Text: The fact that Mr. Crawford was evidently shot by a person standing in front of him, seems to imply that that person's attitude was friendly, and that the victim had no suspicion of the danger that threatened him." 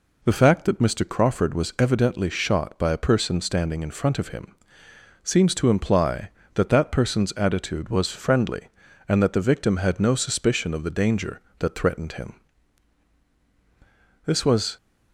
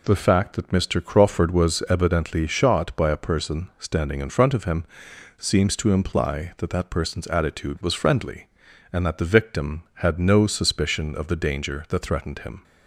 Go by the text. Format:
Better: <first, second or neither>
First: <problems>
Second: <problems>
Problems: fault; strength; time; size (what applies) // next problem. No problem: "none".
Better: second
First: goes on to say "This was"; from 14.2 s on; 0.50 s long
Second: none